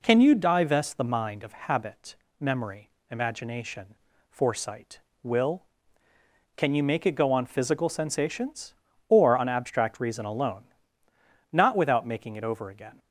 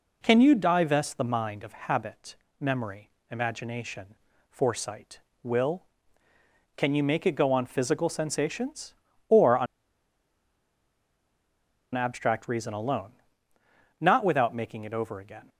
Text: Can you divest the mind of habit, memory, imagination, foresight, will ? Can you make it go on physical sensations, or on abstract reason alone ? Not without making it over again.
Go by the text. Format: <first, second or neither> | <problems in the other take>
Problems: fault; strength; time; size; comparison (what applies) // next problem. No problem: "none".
first | pauses between "on" and "abstract"; strong; at 9.6 s; 2.2 s long